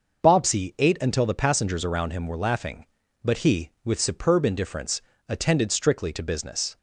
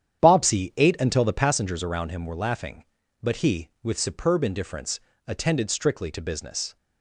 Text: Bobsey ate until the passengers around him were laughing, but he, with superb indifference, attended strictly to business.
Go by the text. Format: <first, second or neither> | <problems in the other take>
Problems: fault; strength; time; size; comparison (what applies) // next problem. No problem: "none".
first | starts louder than the rest; strong; until 1.7 s; 9.5 dB